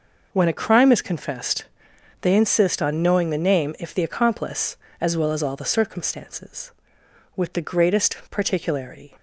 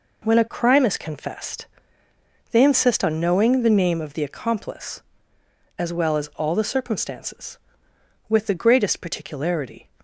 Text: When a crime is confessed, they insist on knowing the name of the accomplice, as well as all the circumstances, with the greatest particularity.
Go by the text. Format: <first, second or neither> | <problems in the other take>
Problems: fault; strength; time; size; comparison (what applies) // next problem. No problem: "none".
second | says "if" for "of"; at 3.7 s